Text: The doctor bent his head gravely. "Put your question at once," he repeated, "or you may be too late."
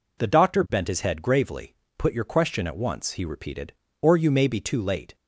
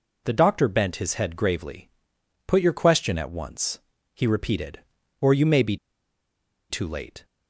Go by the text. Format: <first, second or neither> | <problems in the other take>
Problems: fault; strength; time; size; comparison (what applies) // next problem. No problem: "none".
first | pauses between "be" and "too"; noticeable; at 5.7 s; 0.94 s long